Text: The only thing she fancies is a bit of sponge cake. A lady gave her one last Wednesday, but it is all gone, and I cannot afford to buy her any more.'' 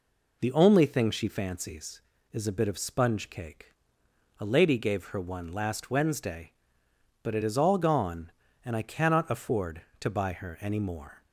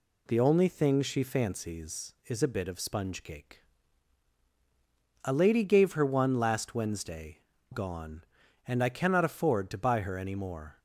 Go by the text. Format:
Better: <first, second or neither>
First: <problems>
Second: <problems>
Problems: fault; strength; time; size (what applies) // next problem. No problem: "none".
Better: first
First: none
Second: skips "but it is all"; at 7.5 s